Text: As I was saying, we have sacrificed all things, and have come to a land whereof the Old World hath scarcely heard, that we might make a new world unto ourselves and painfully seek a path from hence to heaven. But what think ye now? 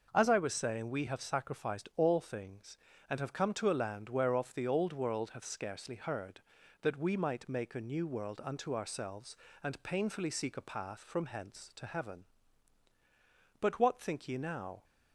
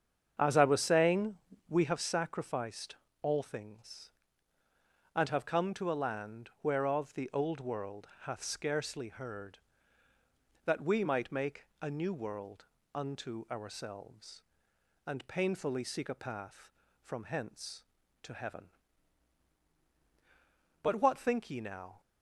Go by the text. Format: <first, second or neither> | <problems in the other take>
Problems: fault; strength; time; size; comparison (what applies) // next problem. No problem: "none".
first | starts louder than the rest; strong; until 2.0 s; 7.5 dB // pauses between "sacrificed" and "all"; slight; at 2.9 s; 0.26 s long // pauses between "World" and "hath"; slight; at 8.0 s; 0.16 s long // pauses between "world" and "unto"; slight; at 12.6 s; 0.28 s long